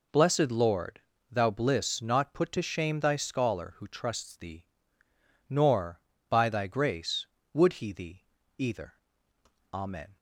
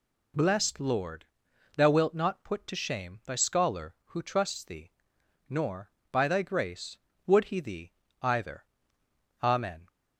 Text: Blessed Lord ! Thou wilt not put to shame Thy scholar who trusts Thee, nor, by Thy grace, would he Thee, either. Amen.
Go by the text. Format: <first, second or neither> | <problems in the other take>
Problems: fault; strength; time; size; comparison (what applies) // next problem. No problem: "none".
second | says "bliss" for "wilt"; at 1.5 s